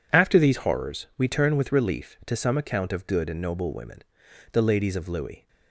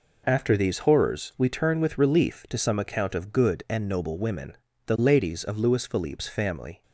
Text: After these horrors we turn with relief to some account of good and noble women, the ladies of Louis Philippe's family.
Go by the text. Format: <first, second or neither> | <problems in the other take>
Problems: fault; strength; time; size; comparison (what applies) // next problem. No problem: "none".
second | stops before "Philippe's family"; at 5.4 s